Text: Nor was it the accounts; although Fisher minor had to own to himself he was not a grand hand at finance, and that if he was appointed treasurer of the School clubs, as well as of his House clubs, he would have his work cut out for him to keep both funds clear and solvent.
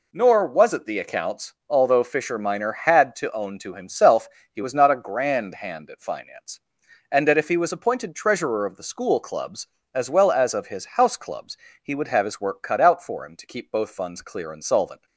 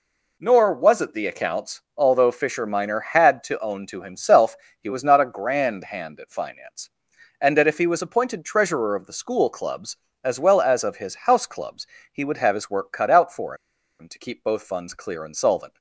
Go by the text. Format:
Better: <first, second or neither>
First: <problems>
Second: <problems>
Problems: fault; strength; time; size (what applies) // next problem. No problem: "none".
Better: first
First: pauses between "himself" and "he"; slight; at 4.2 s; 0.24 s long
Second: pauses between "himself" and "he"; slight; at 4.5 s; 0.24 s long // pauses between "for" and "him"; at 13.5 s; 0.45 s long